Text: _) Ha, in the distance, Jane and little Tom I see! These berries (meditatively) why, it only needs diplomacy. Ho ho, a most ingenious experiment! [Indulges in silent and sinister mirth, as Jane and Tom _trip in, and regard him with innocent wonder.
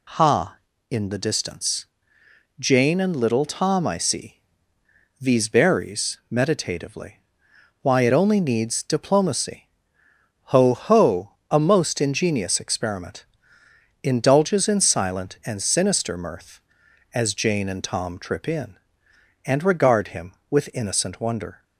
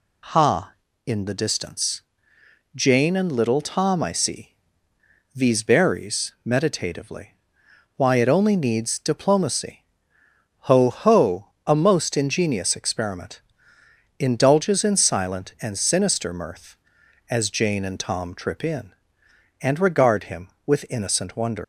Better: first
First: none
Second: leaves "wonder" unfinished; at 21.6 s; 140 ms

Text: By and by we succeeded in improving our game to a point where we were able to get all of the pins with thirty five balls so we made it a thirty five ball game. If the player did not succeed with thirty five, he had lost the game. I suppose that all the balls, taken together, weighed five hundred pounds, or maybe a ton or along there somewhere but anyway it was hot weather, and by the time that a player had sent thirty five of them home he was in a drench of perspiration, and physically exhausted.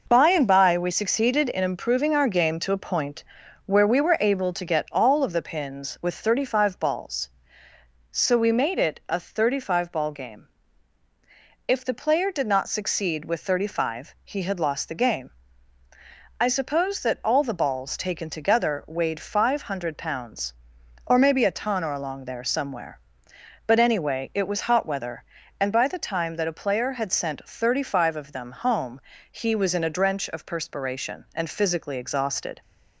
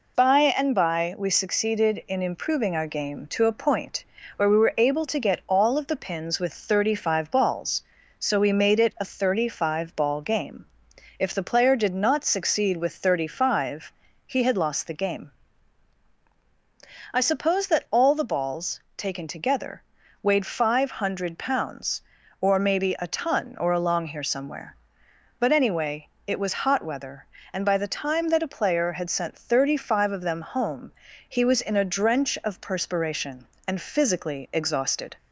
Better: first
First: pauses between "point" and "where"; at 3.2 s; 0.40 s long // pauses between "home" and "he"; slight; at 29.0 s; 0.28 s long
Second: pauses between "point" and "where"; slight; at 4.0 s; 0.32 s long // says "here" for "there"; at 24.0 s // pauses between "anyway" and "it"; slight; at 26.0 s; 0.18 s long // pauses between "home" and "he"; at 30.9 s; 0.38 s long

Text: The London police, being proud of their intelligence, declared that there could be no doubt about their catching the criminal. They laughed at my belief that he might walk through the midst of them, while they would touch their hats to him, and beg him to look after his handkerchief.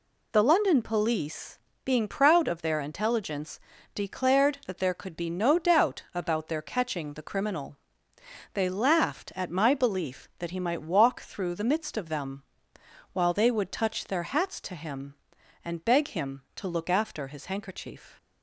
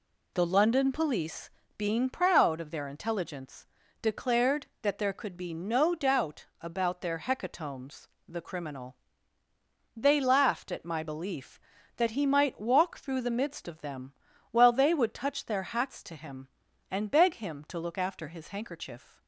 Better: first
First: none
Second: says "hecatombs" for "catching"; at 7.1 s

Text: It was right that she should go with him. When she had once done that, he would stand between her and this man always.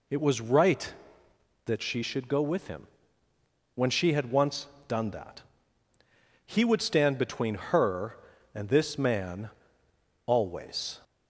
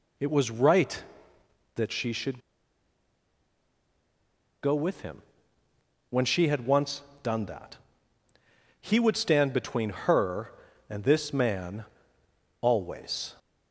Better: first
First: pauses between "once" and "done"; slight; at 4.6 s; 0.22 s long // pauses between "man" and "always"; noticeable; at 9.4 s; 0.78 s long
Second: pauses between "should" and "go"; strong; at 2.3 s; 2.2 s long // pauses between "once" and "done"; slight; at 7.0 s; 0.22 s long // pauses between "man" and "always"; noticeable; at 11.8 s; 0.78 s long

